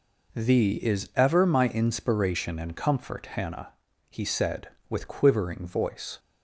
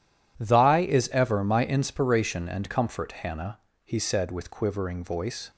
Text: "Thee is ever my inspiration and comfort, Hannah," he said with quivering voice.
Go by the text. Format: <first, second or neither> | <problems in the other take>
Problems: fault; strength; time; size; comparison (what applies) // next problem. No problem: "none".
first | says "Thy" for "Thee"; at 0.4 s